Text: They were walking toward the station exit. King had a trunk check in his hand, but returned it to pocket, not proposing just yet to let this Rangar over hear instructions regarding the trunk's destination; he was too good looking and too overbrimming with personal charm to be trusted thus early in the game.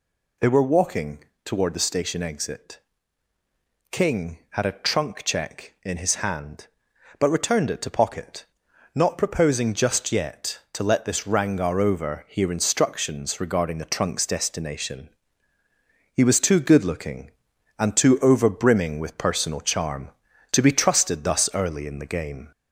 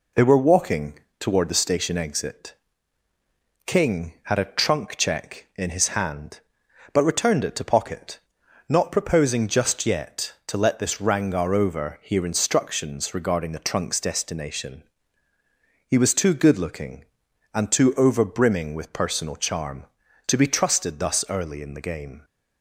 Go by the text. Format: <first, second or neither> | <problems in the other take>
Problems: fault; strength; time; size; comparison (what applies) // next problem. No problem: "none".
second | gets louder; slight; throughout; 2 dB // pauses between "walking" and "toward"; slight; at 1.1 s; 0.24 s long; slight in the second